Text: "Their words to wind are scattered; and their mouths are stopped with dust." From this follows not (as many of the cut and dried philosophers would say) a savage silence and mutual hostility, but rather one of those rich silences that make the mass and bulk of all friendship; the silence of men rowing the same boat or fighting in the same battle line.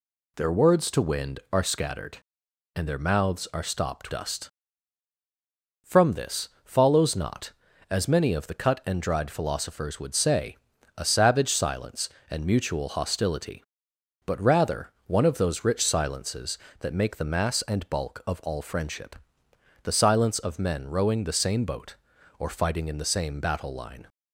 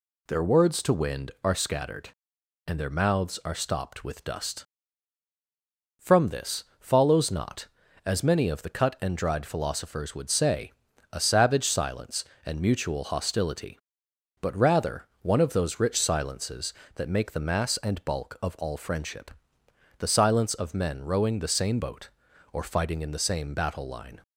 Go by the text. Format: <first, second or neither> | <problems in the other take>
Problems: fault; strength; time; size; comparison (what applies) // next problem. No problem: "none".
second | skips "with"; at 4.1 s // pauses between "this" and "follows"; slight; at 6.4 s; 0.16 s long; slight in the second // pauses between "rather" and "one"; slight; at 14.9 s; 0.16 s long; slight in the second